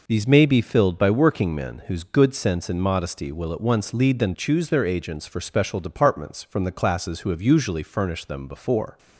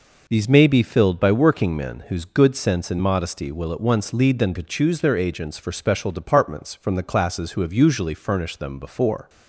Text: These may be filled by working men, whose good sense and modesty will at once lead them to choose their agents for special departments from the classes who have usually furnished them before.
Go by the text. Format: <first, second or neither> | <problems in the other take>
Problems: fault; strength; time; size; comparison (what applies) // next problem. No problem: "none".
second | skips "to"; at 4.3 s